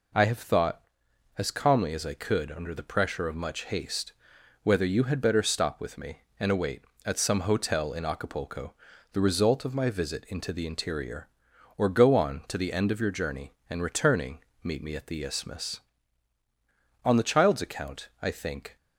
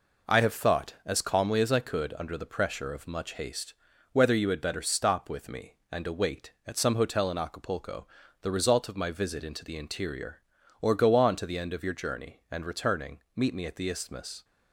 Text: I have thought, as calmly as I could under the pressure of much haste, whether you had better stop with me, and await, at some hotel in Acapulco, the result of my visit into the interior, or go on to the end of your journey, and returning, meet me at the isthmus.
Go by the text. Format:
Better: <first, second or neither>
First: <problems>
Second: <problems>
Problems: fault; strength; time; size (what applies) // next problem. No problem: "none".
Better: second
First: goes on to say "On the child's account I think"; strong; from 17.0 s on; 1.7 s long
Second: none